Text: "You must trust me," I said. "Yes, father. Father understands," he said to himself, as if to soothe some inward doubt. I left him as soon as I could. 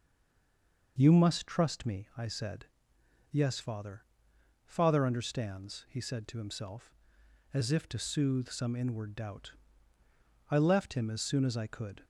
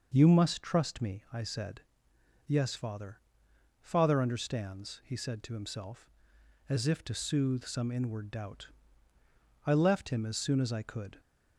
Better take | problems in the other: second | stays silent before the first word; slight; until 0.9 s; 0.9 s long

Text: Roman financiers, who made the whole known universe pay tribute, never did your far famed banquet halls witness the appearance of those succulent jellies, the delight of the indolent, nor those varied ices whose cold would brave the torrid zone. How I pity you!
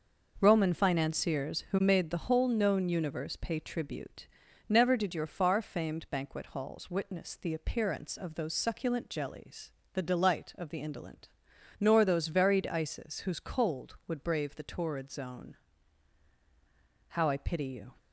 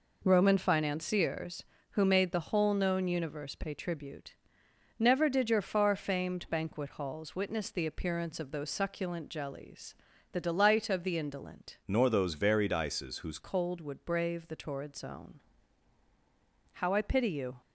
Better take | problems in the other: first | changes voice from "nor" to "whose"; from 11.8 to 13.3 s; 1.5 s long

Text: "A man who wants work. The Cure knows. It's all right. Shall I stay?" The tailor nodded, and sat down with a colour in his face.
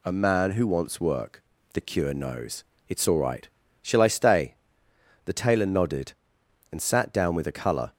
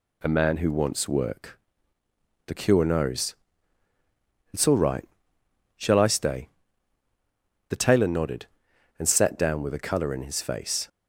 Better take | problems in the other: second | stops before "in his face"; at 7.9 s

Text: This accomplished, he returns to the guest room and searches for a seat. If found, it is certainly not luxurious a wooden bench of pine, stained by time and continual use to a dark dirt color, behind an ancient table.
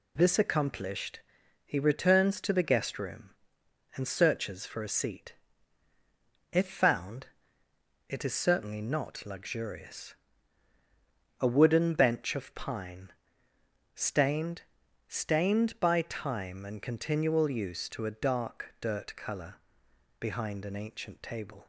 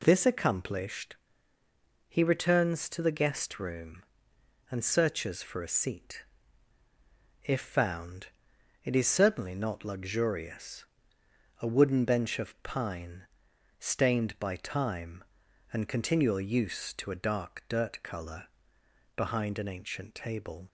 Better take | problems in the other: second | pauses between "luxurious" and "a"; at 10.1 s; 1.2 s long; noticeable in the second // says "stained" twice; at 15.0 s

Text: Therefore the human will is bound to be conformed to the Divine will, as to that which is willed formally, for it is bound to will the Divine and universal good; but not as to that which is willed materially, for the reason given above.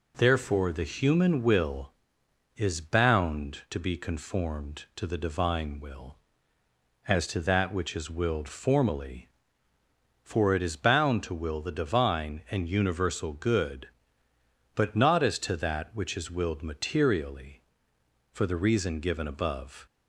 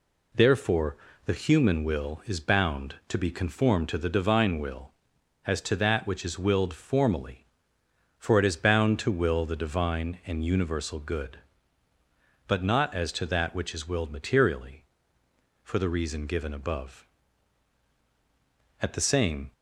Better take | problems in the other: first | pauses between "Therefore" and "the"; slight; at 0.9 s; 0.28 s long // goes on to say "At the same"; noticeable; from 18.8 s on; 0.72 s long

